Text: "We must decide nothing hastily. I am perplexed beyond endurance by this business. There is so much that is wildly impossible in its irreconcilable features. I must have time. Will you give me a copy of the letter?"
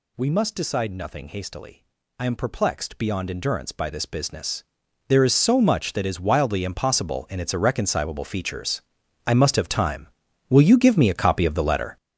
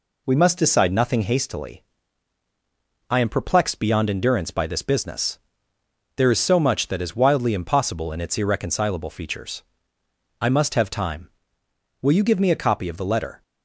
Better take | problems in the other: second | gets louder; strong; throughout; 9.5 dB

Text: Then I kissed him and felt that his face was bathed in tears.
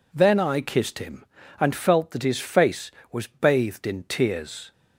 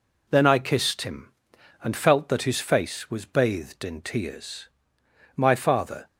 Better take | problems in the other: first | goes on to say "My father"; noticeable; from 5.3 s on; 0.70 s long

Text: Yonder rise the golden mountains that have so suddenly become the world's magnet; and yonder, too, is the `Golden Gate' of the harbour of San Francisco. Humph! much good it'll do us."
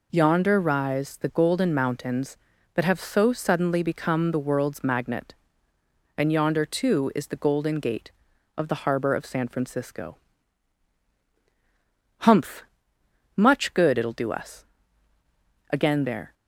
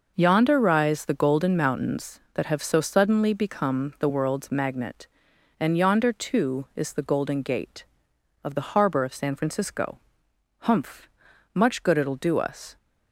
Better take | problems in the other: second | goes on to say "Again there"; from 15.7 s on; 0.60 s long

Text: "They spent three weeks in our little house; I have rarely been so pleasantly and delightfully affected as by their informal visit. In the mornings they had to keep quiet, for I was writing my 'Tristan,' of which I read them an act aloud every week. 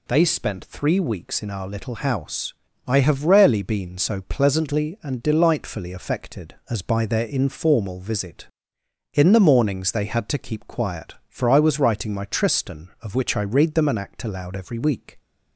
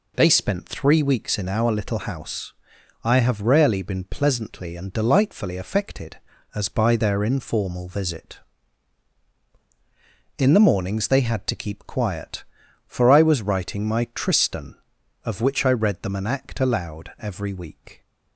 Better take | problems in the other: first | skips "so"; at 4.0 s

